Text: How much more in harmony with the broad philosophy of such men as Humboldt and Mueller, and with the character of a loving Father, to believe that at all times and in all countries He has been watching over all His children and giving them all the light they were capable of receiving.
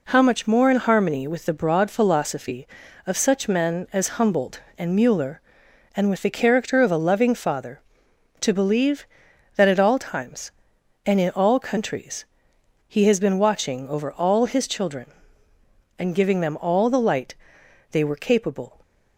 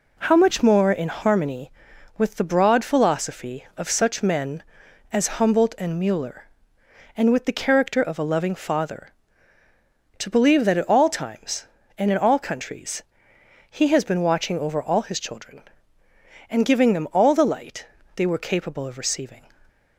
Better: second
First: pauses between "countries" and "He"; noticeable; at 12.2 s; 0.61 s long // pauses between "light" and "they"; noticeable; at 17.3 s; 0.58 s long // stops before "of receiving"; at 18.8 s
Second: pauses between "countries" and "He"; noticeable; at 13.0 s; 0.66 s long // pauses between "light" and "they"; slight; at 17.8 s; 0.30 s long

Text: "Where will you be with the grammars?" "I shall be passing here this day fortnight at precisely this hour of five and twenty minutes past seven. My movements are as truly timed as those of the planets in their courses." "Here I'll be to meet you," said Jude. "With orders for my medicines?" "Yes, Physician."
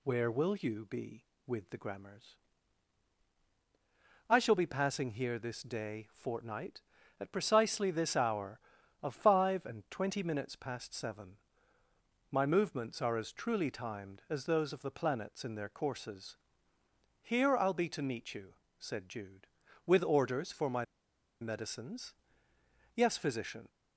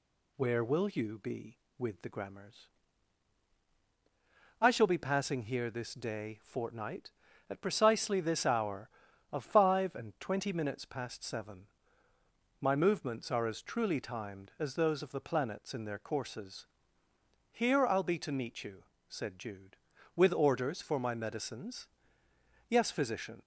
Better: second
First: pauses between "my" and "medicines"; noticeable; at 20.8 s; 0.56 s long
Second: none

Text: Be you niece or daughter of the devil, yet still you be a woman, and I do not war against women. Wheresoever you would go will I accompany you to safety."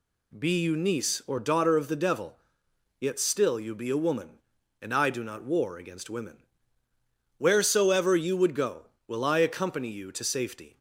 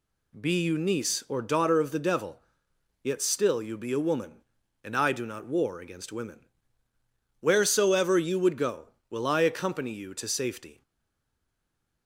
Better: first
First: none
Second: stays silent after the last word; noticeable; from 10.8 s on; 1.2 s long

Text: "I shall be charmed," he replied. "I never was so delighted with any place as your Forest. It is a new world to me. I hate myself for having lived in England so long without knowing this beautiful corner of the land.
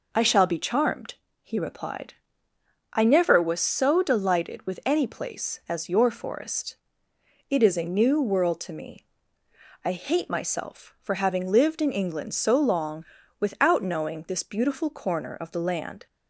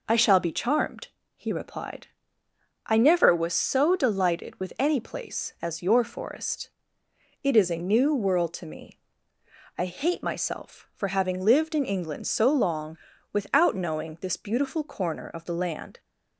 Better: neither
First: pauses between "long" and "without"; slight; at 13.0 s; 0.34 s long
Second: pauses between "long" and "without"; slight; at 12.9 s; 0.34 s long

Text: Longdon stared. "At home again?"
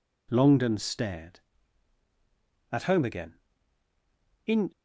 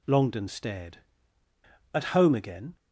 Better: second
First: goes on to say "In"; slight; from 4.4 s on; 0.26 s long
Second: none

